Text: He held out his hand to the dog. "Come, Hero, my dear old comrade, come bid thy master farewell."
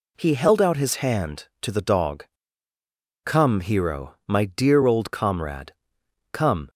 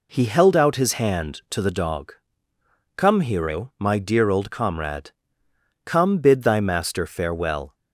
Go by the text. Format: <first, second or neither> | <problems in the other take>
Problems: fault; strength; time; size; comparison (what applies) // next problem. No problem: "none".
second | stops before "bid thy master farewell"; at 6.6 s